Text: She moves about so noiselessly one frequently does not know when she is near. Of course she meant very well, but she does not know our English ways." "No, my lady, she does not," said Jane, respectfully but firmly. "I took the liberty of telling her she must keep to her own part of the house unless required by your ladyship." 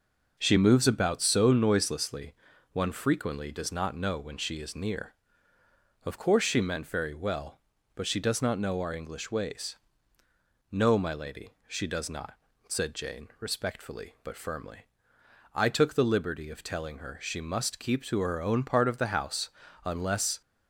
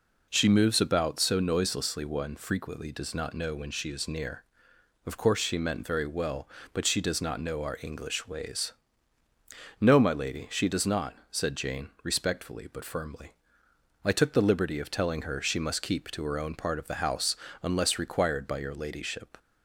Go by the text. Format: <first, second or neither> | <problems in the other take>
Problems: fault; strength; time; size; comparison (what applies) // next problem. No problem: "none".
second | pauses between "noiselessly" and "one"; at 2.3 s; 0.38 s long // pauses between "house" and "unless"; slight; at 19.4 s; 0.36 s long; slight in the second // stops before "required by your ladyship"; at 20.4 s